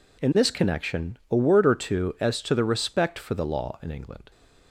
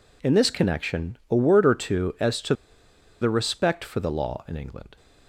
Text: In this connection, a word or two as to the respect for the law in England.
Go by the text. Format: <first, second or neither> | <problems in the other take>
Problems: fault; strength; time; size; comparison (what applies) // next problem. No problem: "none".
first | pauses between "to" and "the"; noticeable; at 2.5 s; 0.67 s long